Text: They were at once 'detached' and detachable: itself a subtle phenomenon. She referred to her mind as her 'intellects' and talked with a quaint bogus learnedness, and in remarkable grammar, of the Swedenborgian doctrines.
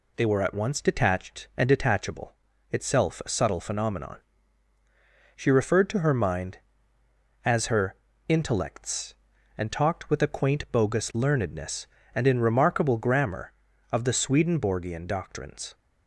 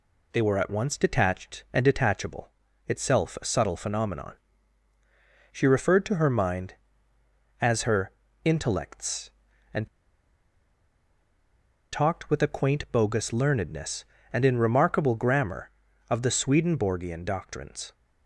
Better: first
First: pauses between "her" and "intellects"; slight; at 7.9 s; 0.32 s long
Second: pauses between "her" and "intellects"; slight; at 8.1 s; 0.32 s long // pauses between "and" and "talked"; strong; at 9.8 s; 2.0 s long

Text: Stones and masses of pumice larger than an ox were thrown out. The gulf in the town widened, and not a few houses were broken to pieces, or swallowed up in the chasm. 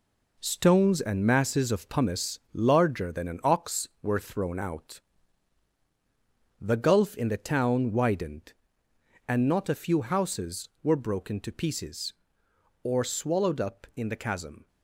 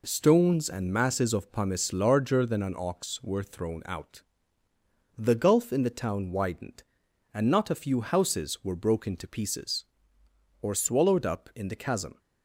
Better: second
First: gets quieter; strong; throughout; 7.5 dB // pauses between "pumice" and "larger"; slight; at 2.3 s; 0.16 s long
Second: none

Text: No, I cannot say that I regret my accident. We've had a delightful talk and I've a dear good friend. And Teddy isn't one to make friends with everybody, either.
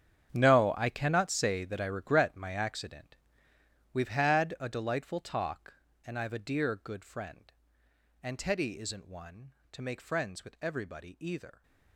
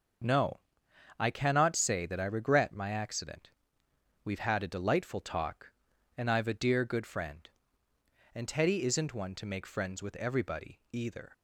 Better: second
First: gets quieter; strong; throughout; 15.5 dB // starts louder than the rest; strong; until 1.3 s; 8.5 dB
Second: starts louder than the rest; until 1.8 s; 6.5 dB

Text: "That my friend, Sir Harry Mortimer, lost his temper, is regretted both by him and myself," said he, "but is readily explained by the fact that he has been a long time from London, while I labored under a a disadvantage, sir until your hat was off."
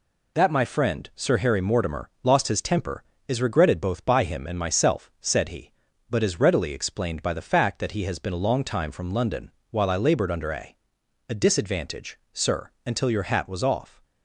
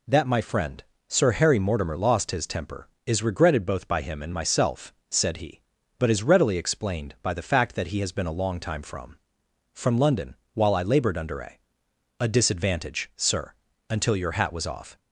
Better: first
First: pauses between "a" and "a"; noticeable; at 10.7 s; 0.54 s long // pauses between "sir" and "until"; slight; at 12.6 s; 0.16 s long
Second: says "from" twice; at 9.7 s // pauses between "a" and "a"; noticeable; at 11.5 s; 0.64 s long // pauses between "sir" and "until"; at 13.5 s; 0.38 s long

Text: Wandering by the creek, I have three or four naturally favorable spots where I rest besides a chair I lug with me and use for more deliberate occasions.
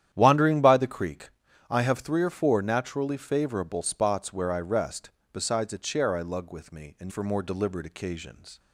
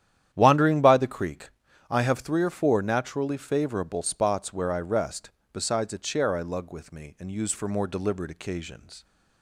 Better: second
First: starts louder than the rest; strong; until 1.1 s; 10.5 dB // pauses between "rest" and "besides"; slight; at 5.0 s; 0.24 s long // skips "use"; at 7.0 s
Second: starts louder than the rest; strong; until 1.3 s; 10.5 dB // pauses between "rest" and "besides"; slight; at 5.2 s; 0.24 s long

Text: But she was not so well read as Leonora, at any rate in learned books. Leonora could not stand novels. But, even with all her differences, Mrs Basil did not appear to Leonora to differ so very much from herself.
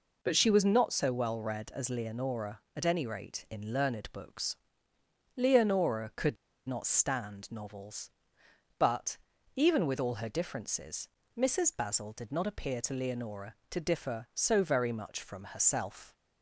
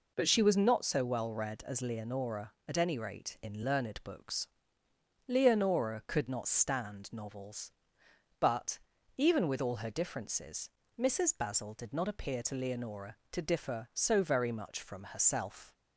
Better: second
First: pauses between "could" and "not"; slight; at 6.3 s; 0.31 s long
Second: none

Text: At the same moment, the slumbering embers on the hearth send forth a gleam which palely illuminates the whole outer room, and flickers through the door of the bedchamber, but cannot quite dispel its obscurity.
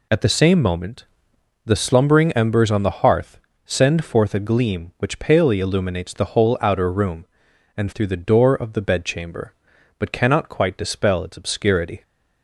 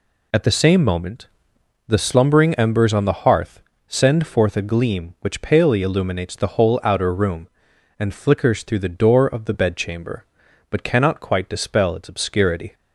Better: second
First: pauses between "hearth" and "send"; slight; at 3.4 s; 0.26 s long // skips "flickers"; at 7.9 s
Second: pauses between "hearth" and "send"; slight; at 3.6 s; 0.26 s long

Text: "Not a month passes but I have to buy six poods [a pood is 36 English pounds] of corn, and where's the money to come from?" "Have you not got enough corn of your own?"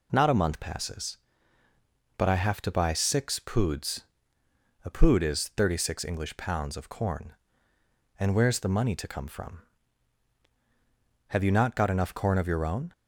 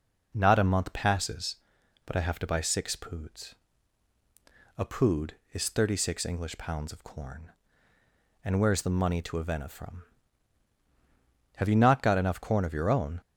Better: first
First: pauses between "poods" and "a"; noticeable; at 4.0 s; 0.80 s long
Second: pauses between "poods" and "a"; at 3.5 s; 1.2 s long // says "avena" for "come"; at 9.3 s

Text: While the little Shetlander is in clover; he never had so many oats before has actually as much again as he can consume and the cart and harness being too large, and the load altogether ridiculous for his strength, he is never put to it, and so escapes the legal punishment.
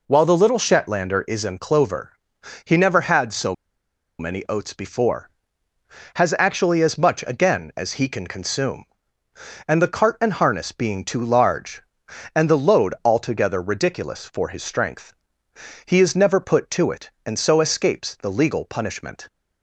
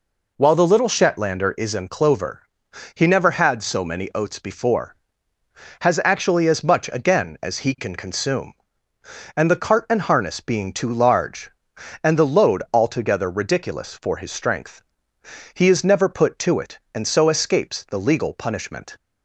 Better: second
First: pauses between "so" and "many"; noticeable; at 3.5 s; 0.64 s long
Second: none

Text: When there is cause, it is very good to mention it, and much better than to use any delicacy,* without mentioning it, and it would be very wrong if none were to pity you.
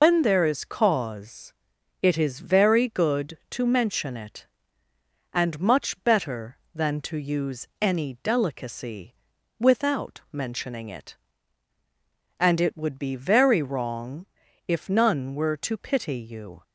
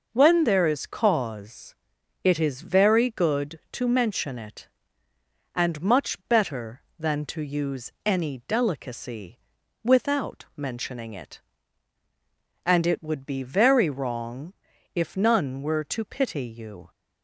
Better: second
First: loses the start of "When"; at 0.0 s; 120 ms // pauses between "wrong" and "if"; at 14.2 s; 0.42 s long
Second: pauses between "wrong" and "if"; at 14.5 s; 0.42 s long

